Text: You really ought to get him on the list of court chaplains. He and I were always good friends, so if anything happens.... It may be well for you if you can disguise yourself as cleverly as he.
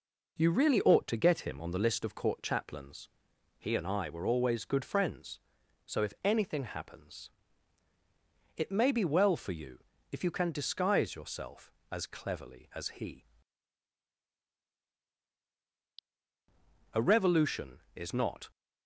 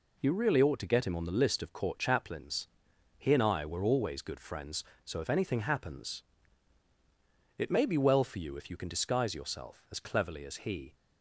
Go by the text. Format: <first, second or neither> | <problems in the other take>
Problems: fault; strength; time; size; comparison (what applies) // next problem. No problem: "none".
second | pauses between "you" and "if"; slight; at 9.8 s; 0.32 s long // goes on to say "A revolution is not"; from 16.9 s on; 1.5 s long